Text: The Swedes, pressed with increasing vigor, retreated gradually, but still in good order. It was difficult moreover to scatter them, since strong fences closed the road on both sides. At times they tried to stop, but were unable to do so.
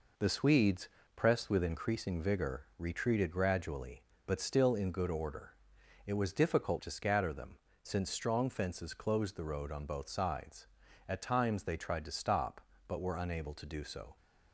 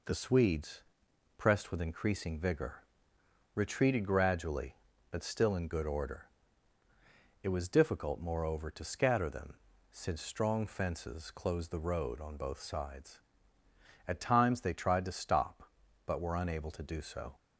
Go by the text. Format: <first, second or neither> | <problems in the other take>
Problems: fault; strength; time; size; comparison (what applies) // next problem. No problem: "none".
second | skips "moreover"; at 6.7 s